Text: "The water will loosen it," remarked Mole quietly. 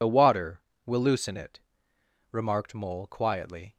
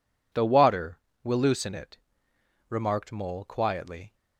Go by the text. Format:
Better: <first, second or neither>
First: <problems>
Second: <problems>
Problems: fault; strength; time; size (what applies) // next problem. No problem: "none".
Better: second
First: loses the start of "The"; at 0.0 s; 50 ms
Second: none